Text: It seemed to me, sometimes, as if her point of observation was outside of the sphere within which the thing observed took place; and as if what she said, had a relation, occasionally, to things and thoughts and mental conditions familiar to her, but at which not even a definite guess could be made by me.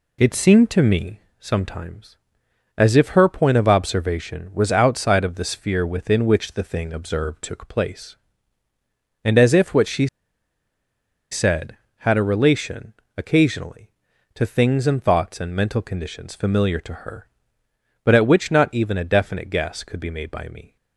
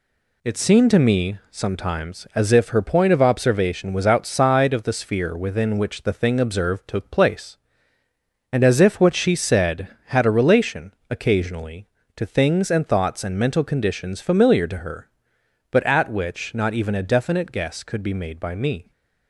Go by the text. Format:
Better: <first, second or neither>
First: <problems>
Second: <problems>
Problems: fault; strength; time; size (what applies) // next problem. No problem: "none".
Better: second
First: pauses between "she" and "said"; at 10.0 s; 1.2 s long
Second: none